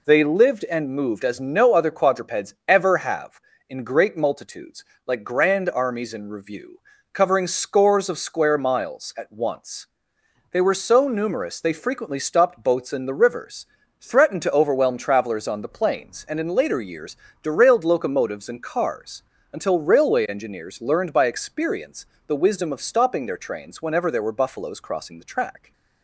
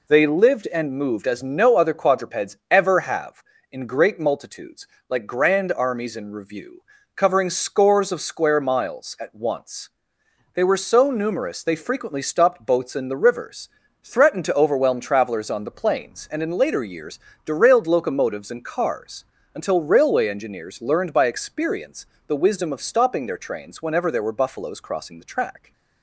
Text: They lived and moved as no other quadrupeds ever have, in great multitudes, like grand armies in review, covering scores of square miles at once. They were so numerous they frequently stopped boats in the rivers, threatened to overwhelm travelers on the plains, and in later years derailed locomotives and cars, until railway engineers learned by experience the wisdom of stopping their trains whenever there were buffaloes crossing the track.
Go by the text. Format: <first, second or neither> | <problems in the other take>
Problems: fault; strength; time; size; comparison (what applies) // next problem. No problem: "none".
neither | pauses between "years" and "derailed"; slight; the same in both // pauses between "experience" and "the"; slight; the same in both